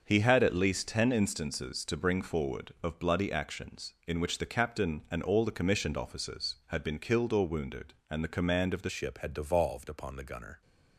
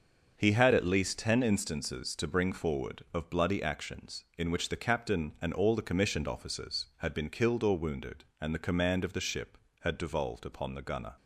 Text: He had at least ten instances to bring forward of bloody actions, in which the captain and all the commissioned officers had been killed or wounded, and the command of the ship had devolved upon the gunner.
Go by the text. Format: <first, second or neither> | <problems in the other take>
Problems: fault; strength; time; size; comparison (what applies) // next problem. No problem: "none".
second | starts louder than the rest; until 1.0 s; 6.5 dB; also in the second // changes voice at "ship"; from 8.8 s on; 1.8 s long